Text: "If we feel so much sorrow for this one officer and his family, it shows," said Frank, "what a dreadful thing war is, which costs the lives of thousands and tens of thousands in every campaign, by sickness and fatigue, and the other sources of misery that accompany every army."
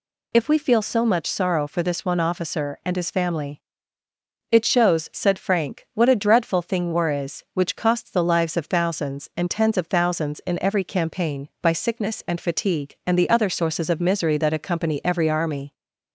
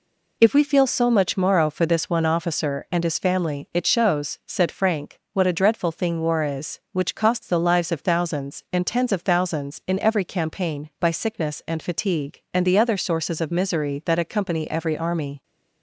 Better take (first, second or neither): first